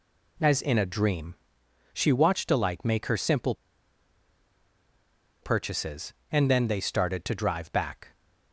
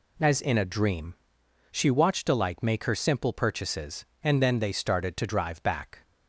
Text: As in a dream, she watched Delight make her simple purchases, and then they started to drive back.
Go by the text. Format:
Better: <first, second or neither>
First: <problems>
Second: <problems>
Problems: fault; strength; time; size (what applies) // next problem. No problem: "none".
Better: second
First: pauses between "simple" and "purchases"; strong; at 3.5 s; 1.8 s long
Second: none